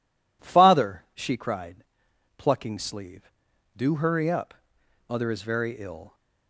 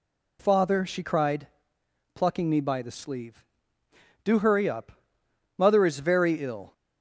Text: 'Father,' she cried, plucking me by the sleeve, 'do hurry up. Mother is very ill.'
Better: second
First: skips "me by the"; at 2.7 s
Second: none

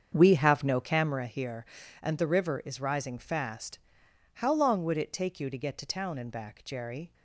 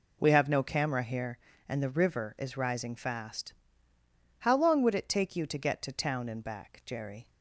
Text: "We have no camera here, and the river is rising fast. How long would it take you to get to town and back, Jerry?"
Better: second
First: starts louder than the rest; strong; until 1.3 s; 7.5 dB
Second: none

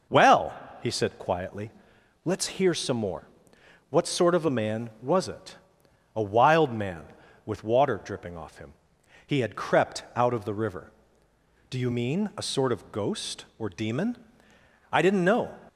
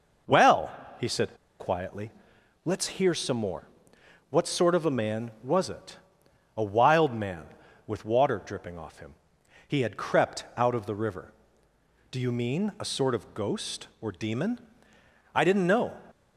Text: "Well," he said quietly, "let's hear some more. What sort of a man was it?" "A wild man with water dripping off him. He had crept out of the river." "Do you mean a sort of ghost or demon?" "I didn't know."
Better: first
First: none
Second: pauses between "said" and "quietly"; slight; at 1.3 s; 0.24 s long

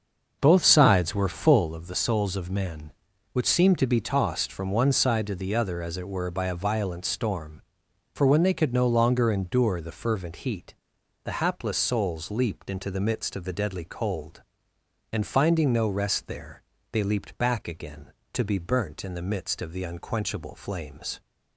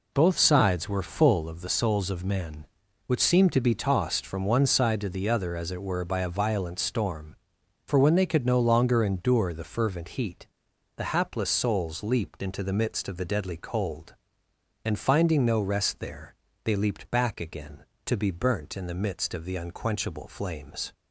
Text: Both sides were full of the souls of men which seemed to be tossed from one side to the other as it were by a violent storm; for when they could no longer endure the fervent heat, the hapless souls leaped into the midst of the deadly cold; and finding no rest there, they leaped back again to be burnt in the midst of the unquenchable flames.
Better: second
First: starts louder than the rest; until 1.7 s; 6.5 dB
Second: none

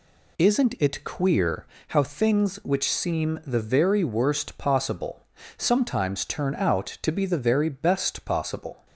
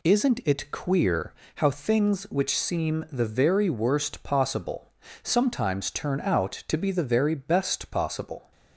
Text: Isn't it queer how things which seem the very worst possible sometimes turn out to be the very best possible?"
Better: neither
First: pauses between "queer" and "how"; slight; at 1.6 s; 0.26 s long // pauses between "possible" and "sometimes"; slight; at 5.2 s; 0.32 s long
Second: pauses between "queer" and "how"; slight; at 1.3 s; 0.26 s long // pauses between "possible" and "sometimes"; slight; at 4.9 s; 0.32 s long

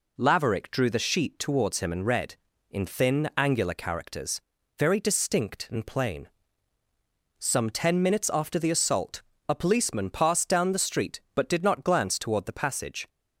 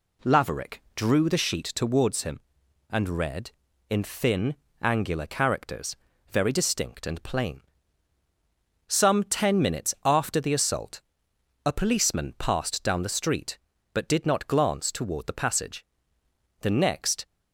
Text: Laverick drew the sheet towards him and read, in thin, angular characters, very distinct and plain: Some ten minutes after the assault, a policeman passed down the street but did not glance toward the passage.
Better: first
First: none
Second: goes on to say "The next"; noticeable; from 16.5 s on; 0.66 s long

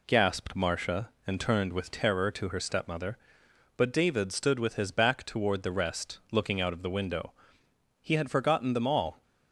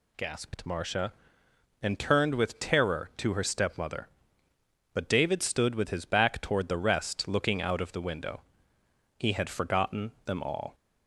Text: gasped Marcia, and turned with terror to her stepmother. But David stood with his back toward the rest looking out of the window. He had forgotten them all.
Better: neither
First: none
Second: none

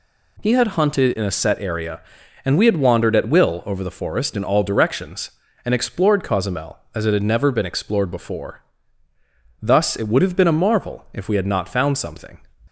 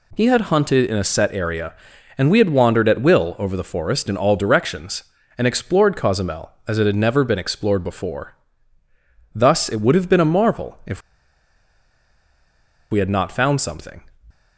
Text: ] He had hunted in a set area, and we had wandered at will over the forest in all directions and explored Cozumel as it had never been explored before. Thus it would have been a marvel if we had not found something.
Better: first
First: none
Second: pauses between "if" and "we"; strong; at 10.9 s; 1.9 s long

